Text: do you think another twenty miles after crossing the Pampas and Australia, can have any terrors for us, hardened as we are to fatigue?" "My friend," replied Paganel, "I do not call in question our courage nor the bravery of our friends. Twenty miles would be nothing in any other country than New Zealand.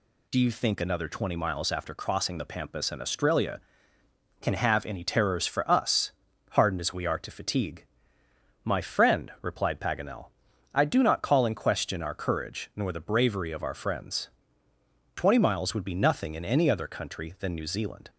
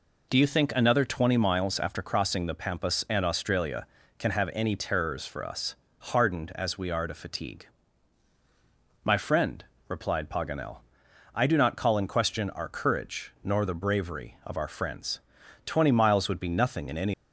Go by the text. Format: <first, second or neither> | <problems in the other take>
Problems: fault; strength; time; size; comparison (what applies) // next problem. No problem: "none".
first | stops before "other country than New Zealand"; at 17.1 s